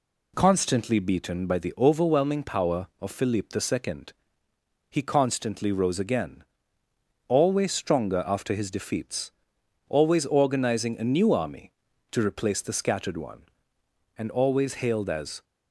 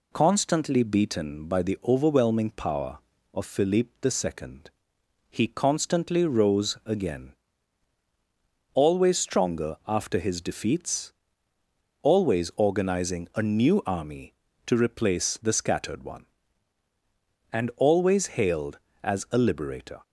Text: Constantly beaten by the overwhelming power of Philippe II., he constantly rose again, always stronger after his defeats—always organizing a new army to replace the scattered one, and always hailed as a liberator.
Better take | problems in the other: second | stops before "a liberator"; at 15.4 s

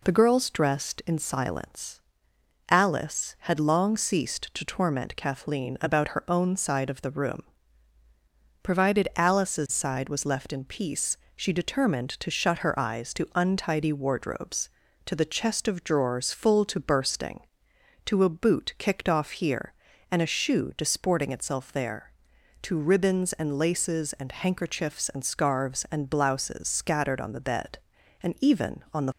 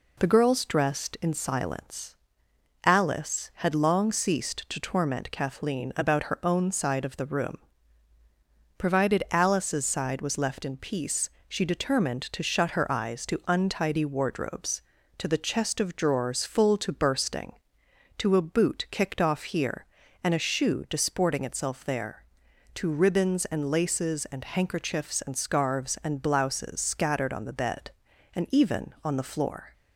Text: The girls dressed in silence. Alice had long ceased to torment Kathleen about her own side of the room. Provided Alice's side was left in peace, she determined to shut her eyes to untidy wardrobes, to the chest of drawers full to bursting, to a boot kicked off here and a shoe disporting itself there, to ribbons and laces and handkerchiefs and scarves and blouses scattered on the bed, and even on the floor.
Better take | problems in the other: second | stops before "floor"; at 29.1 s

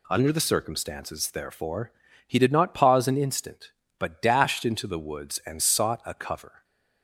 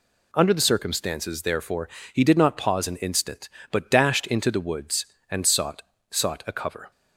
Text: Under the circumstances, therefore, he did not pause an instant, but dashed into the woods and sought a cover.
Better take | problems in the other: first | says "sought" twice; at 6.1 s

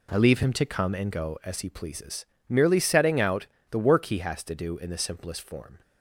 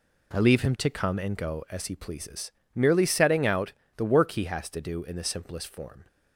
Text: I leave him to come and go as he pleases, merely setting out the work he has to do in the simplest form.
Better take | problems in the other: neither | pauses between "out" and "the"; slight; the same in both

